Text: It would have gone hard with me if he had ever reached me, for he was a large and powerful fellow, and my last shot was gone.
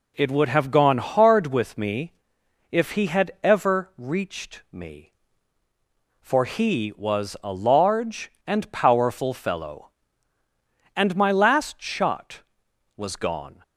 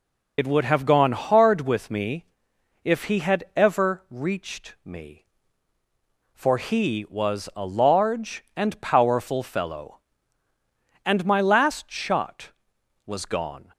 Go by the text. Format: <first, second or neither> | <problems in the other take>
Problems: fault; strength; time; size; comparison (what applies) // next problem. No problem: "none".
first | loses the start of "It"; at 0.3 s; 75 ms // pauses between "me" and "if"; noticeable; at 2.2 s; 0.58 s long; noticeable in the first